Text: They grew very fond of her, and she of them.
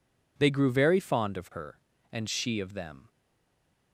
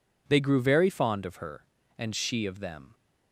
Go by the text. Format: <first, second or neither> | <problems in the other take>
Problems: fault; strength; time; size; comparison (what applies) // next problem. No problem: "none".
second | stays silent after the last word; slight; from 3.0 s on; 0.9 s long